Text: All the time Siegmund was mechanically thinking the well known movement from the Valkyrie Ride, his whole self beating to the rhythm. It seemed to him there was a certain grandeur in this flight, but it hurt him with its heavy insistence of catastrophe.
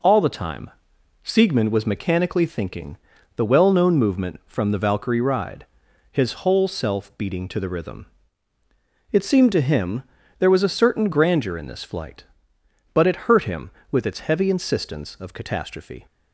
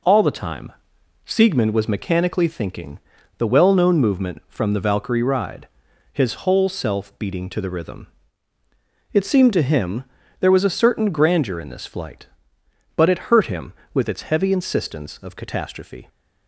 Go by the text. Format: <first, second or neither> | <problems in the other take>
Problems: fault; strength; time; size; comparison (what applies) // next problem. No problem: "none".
neither | pauses between "time" and "Siegmund"; noticeable; the same in both // pauses between "thinking" and "the"; the same in both // pauses between "him" and "there"; slight; the same in both